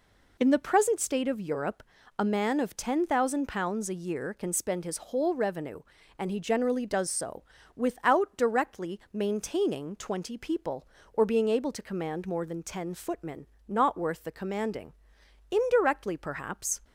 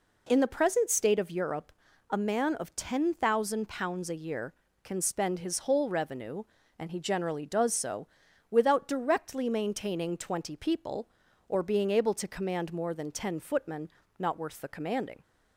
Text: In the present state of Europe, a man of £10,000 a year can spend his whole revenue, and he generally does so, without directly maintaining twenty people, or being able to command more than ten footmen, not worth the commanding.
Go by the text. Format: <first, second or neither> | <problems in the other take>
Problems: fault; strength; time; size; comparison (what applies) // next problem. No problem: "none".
second | goes on to say "Indirectly perhaps"; noticeable; from 15.5 s on; 1.3 s long